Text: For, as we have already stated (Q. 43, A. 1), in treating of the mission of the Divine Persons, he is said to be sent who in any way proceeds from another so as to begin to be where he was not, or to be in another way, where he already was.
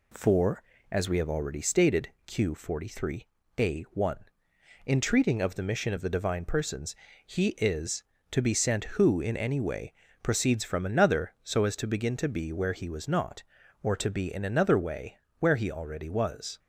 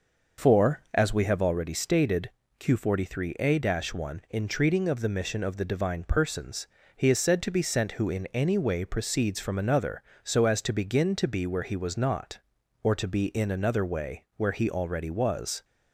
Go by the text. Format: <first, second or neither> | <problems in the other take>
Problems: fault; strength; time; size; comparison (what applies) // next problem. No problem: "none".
second | skips "said"; at 8.1 s // pauses between "way" and "proceeds"; slight; at 9.9 s; 0.28 s long